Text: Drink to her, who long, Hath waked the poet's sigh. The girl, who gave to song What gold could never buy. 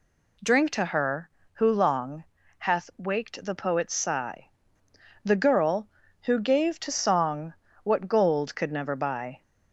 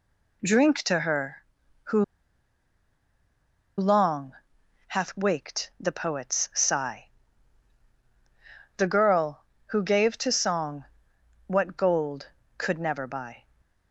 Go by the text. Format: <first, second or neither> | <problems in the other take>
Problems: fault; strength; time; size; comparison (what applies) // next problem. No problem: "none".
first | pauses between "who" and "long"; strong; at 2.0 s; 1.7 s long // pauses between "song" and "What"; noticeable; at 10.8 s; 0.62 s long; slight in the first // stays silent after the last word; slight; from 13.4 s on; 0.5 s long